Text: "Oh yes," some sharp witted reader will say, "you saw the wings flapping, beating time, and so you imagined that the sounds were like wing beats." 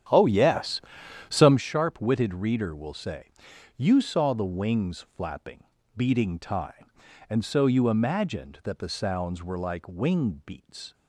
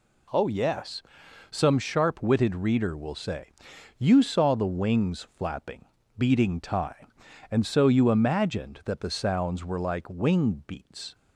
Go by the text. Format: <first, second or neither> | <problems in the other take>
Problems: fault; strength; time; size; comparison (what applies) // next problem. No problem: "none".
second | starts louder than the rest; strong; until 1.6 s; 9.5 dB